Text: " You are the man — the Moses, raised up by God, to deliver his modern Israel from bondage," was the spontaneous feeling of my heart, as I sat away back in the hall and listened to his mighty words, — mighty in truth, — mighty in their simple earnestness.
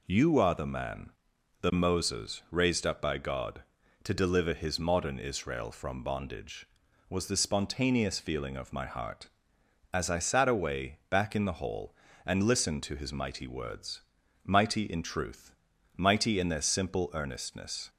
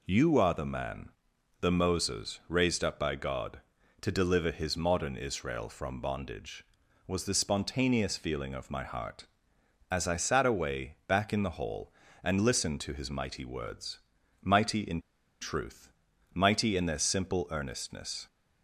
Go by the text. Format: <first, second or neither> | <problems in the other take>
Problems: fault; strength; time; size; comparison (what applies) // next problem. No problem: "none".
first | pauses between "in" and "truth"; at 14.9 s; 0.42 s long